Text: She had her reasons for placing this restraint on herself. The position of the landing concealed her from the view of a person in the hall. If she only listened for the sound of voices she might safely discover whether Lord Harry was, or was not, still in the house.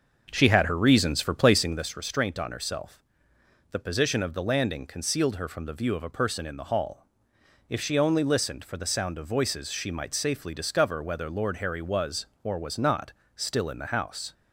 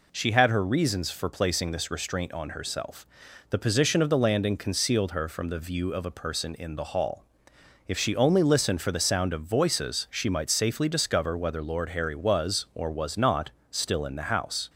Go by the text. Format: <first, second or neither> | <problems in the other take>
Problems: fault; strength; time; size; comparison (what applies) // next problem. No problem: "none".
second | starts louder than the rest; until 1.9 s; 6 dB